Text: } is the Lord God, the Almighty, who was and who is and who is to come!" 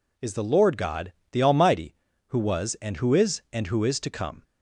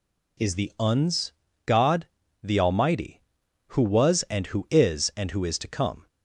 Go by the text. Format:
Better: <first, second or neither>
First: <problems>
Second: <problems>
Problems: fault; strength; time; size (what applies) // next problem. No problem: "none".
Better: first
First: none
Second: says "Uns" for "Lord"; at 0.7 s